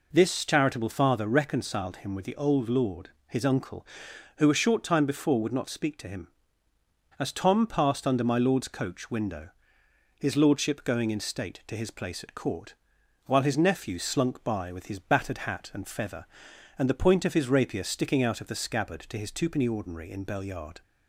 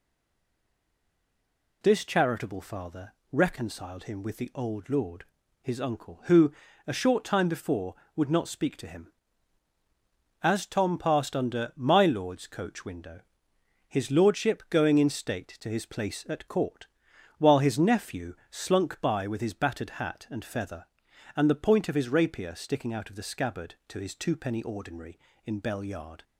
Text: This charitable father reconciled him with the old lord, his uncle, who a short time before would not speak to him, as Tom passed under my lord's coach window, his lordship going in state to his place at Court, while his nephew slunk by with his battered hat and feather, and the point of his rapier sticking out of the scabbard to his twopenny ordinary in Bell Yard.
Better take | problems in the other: first | stays silent before the first word; noticeable; until 1.8 s; 1.8 s long // pauses between "father" and "reconciled"; slight; at 3.1 s; 0.18 s long // pauses between "who" and "a"; slight; at 6.5 s; 0.34 s long

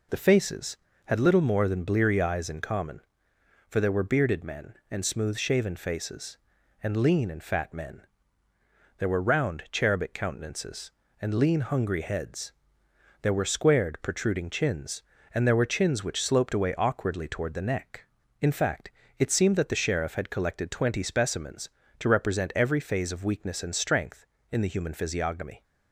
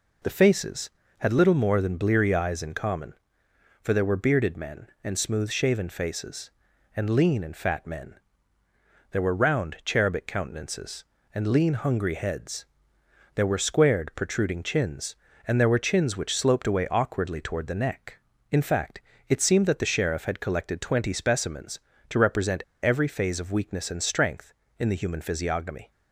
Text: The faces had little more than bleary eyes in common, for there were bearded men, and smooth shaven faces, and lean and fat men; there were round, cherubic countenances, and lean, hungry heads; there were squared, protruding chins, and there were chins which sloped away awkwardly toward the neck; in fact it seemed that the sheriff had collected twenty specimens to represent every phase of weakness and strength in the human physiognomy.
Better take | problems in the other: first | pauses between "fact" and "it"; slight; at 19.0 s; 0.26 s long; slight in the first // pauses between "represent" and "every"; slight; at 22.6 s; 0.19 s long

